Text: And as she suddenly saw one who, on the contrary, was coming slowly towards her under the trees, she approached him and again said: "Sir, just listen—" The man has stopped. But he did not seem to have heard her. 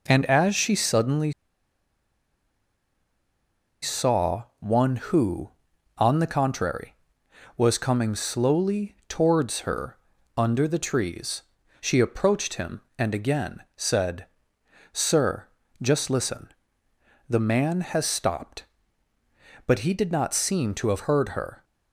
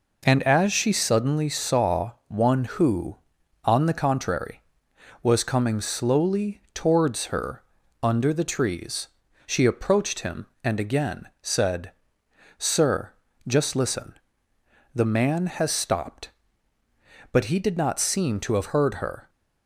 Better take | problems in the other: second | pauses between "suddenly" and "saw"; strong; at 1.3 s; 2.4 s long // pauses between "saw" and "one"; slight; at 4.4 s; 0.16 s long; slight in the second // pauses between "her" and "under"; at 9.9 s; 0.40 s long; also in the second

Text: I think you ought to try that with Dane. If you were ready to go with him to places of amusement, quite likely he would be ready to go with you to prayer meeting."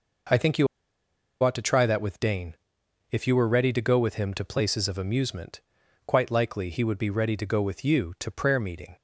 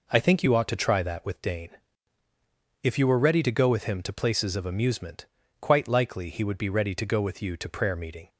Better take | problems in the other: second | pauses between "you" and "ought"; noticeable; at 0.6 s; 0.76 s long

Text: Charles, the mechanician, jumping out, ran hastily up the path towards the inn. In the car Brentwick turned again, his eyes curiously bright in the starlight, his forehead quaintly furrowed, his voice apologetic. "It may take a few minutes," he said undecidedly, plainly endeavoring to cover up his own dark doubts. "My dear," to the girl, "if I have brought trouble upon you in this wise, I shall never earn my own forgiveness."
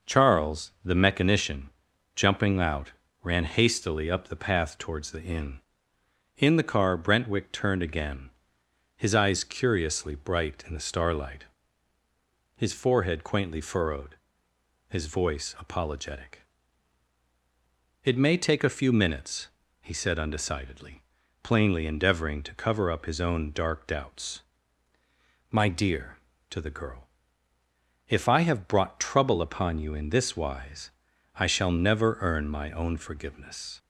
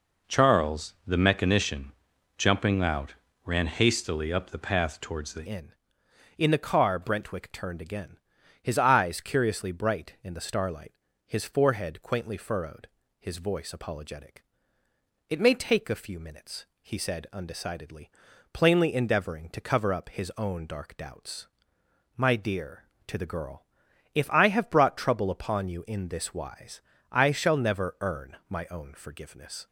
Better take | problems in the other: first | changes voice at "inn"; from 5.4 s on; 24.2 s long

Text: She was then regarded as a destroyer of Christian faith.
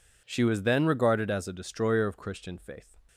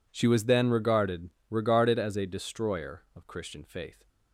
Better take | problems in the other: first | says "regarded" twice; at 1.5 s

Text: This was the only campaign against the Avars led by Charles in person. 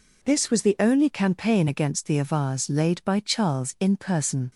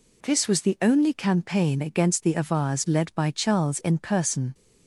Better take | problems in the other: second | says "laid" for "led"; at 2.6 s

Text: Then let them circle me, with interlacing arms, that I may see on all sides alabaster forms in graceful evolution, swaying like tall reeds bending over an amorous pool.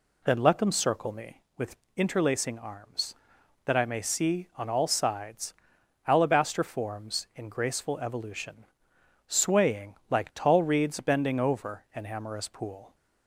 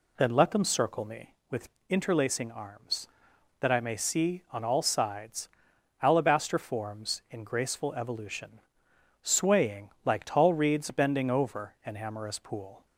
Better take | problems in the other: neither | pauses between "with" and "interlacing"; slight; the same in both // pauses between "sides" and "alabaster"; noticeable; the same in both

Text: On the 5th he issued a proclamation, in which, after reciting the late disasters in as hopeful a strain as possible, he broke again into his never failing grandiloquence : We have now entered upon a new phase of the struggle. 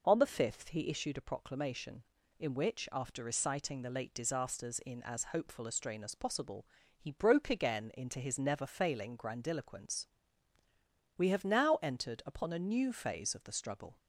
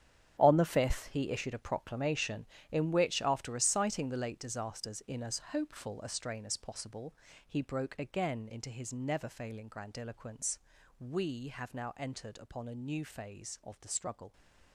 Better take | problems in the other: first | gets quieter; strong; throughout; 12.5 dB

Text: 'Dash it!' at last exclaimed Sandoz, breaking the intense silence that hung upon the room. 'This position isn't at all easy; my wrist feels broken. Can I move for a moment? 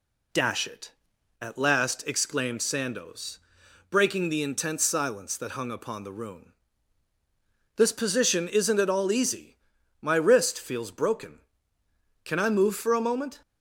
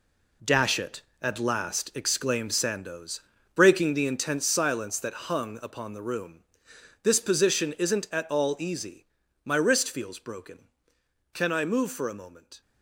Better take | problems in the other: first | gets quieter; strong; throughout; 10.5 dB

